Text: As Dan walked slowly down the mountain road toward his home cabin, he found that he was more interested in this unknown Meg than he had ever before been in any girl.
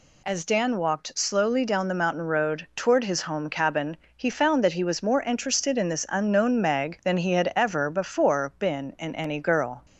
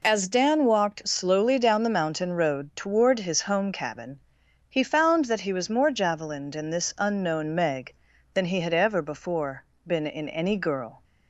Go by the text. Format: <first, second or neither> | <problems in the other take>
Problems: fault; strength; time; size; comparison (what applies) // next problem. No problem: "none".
first | says "javelined" for "interested"; at 5.9 s // pauses between "before" and "been"; slight; at 9.6 s; 0.24 s long